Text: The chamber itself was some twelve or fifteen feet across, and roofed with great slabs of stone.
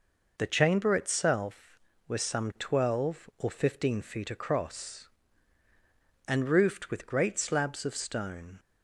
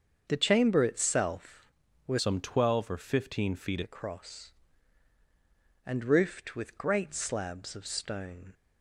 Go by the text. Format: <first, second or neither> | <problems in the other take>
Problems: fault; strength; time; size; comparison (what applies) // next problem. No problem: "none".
first | starts louder than the rest; until 1.3 s; 7 dB // changes voice from "some" to "feet"; from 2.1 to 3.8 s; 1.7 s long